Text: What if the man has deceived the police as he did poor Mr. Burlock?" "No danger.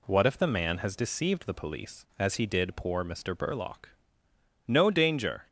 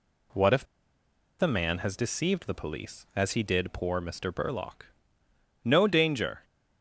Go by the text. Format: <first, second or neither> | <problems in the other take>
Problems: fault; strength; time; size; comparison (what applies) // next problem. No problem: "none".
first | pauses between "if" and "the"; noticeable; at 0.6 s; 0.76 s long